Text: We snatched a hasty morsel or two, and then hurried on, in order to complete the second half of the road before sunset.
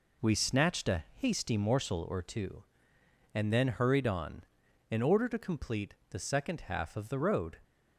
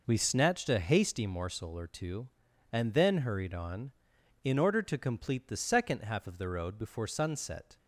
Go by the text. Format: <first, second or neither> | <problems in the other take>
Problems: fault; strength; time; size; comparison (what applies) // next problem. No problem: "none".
second | pauses between "complete" and "the"; slight; at 5.9 s; 0.16 s long // stops before "before sunset"; at 7.6 s